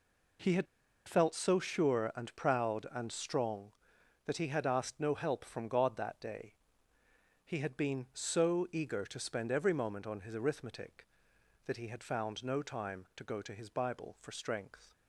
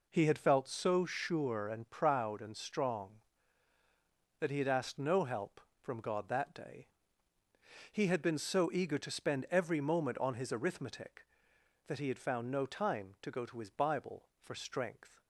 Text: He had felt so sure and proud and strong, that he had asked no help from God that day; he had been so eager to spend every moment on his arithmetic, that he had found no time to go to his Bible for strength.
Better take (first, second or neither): second